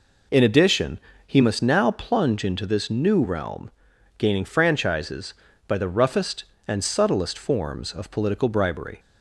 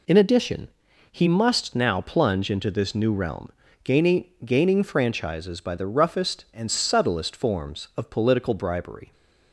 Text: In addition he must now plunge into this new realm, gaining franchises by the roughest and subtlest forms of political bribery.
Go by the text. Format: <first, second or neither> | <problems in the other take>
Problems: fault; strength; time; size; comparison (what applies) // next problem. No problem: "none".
first | pauses between "addition" and "he"; at 0.6 s; 0.42 s long; slight in the first // says "gaining" twice; at 4.4 s